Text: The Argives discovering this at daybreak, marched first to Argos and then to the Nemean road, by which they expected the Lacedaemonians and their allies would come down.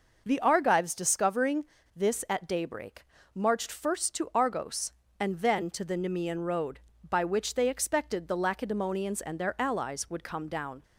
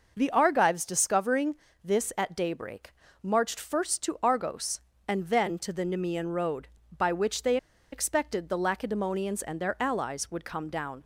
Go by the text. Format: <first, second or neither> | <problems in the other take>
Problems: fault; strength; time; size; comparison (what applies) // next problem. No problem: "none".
first | pauses between "discovering" and "this"; slight; at 1.5 s; 0.30 s long; slight in the first // pauses between "they" and "expected"; slight; at 7.5 s; 0.36 s long